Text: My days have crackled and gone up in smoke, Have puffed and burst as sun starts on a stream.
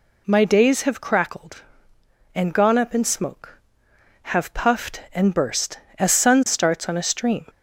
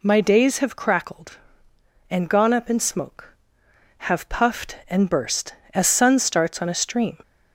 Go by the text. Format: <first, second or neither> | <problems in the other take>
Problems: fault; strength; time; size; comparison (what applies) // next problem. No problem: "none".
neither | none